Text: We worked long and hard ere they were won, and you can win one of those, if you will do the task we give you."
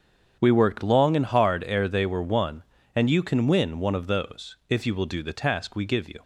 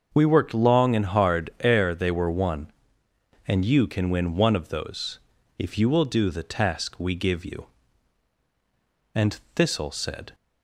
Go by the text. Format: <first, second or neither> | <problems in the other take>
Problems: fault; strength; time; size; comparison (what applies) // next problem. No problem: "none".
first | starts louder than the rest; until 1.1 s; 6.5 dB; strong in the first // goes on to say "And Thistle said"; noticeable; from 9.1 s on; 1.2 s long